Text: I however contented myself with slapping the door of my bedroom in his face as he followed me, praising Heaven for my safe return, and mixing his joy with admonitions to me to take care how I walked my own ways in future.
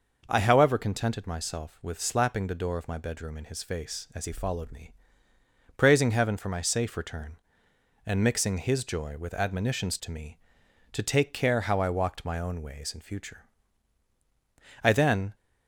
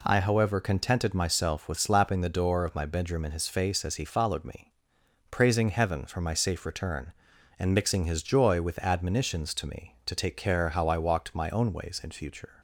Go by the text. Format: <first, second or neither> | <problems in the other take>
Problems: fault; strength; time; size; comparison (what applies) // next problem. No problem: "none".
second | goes on to say "I then"; from 14.8 s on; 0.52 s long